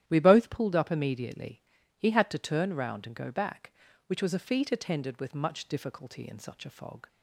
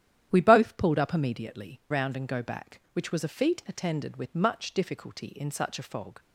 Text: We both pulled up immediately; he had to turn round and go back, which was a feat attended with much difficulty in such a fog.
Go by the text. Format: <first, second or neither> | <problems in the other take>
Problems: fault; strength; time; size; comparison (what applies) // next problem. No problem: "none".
first | starts louder than the rest; strong; until 1.3 s; 11 dB; strong in the first // skips "he had to turn"; at 1.8 s